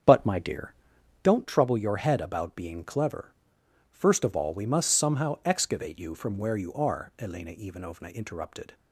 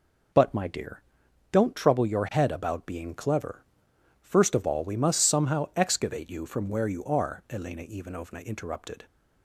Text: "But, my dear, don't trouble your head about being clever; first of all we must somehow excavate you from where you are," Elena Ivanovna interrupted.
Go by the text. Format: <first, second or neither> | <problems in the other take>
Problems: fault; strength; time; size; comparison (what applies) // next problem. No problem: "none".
second | starts louder than the rest; strong; until 1.3 s; 7.5 dB